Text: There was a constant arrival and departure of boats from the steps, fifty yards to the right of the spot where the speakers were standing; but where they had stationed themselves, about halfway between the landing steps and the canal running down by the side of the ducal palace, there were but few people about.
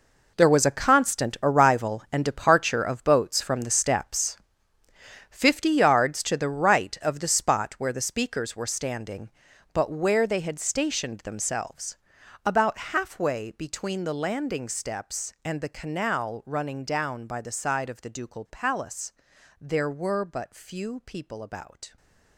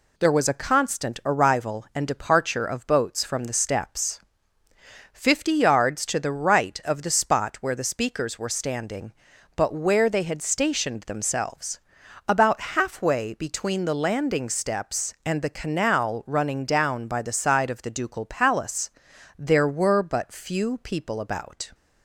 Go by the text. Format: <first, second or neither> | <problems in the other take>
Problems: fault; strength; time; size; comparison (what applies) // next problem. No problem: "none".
second | gets quieter; strong; throughout; 13 dB